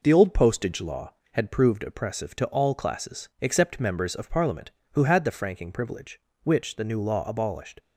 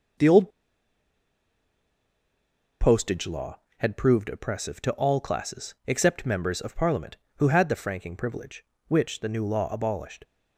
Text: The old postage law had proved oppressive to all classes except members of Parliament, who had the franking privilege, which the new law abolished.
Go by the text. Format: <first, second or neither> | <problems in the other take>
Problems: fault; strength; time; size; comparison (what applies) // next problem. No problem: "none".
first | pauses between "old" and "postage"; strong; at 0.4 s; 2.3 s long